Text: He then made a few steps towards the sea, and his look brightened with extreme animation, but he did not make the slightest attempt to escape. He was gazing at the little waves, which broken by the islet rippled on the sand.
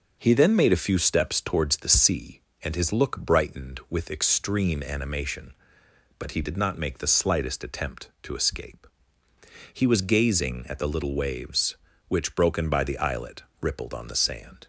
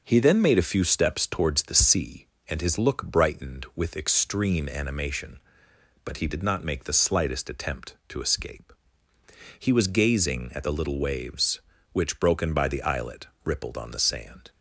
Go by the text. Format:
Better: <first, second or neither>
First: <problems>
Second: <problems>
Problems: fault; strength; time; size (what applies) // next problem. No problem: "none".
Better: neither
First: starts louder than the rest; noticeable; until 1.2 s; 6 dB // pauses between "islet" and "rippled"; slight; at 13.4 s; 0.18 s long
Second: starts louder than the rest; noticeable; until 1.0 s; 6 dB // pauses between "islet" and "rippled"; slight; at 13.2 s; 0.18 s long